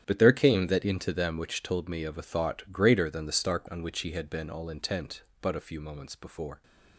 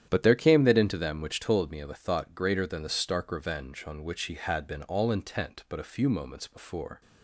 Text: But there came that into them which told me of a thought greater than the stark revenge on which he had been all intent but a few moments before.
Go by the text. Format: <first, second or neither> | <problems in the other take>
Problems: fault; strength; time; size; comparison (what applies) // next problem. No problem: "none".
second | starts louder than the rest; strong; until 1.0 s; 10 dB; strong in the second // skips "revenge"; at 3.6 s